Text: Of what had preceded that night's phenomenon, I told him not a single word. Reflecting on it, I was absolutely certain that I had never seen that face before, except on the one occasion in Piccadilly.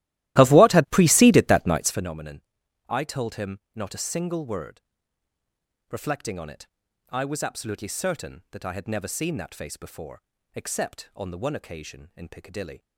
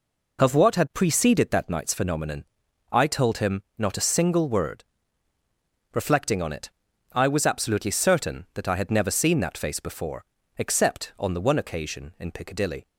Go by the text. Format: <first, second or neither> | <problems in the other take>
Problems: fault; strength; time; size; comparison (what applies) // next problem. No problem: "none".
second | starts louder than the rest; strong; until 2.1 s; 15.5 dB // pauses between "him" and "not"; slight; at 3.5 s; 0.16 s long; slight in the second